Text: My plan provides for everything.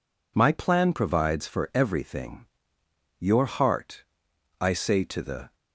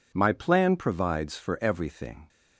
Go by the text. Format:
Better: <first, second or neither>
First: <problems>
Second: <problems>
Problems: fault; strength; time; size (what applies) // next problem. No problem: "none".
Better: second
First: goes on to say "Your heart I say to the"; strong; from 3.2 s on; 2.3 s long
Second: none